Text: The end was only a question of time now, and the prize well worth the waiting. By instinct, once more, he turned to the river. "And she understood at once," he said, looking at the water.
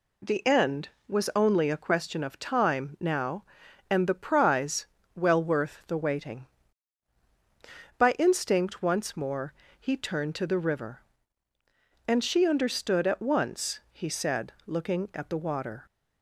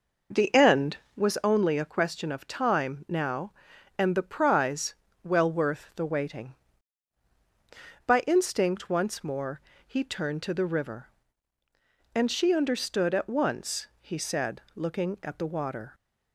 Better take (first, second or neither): first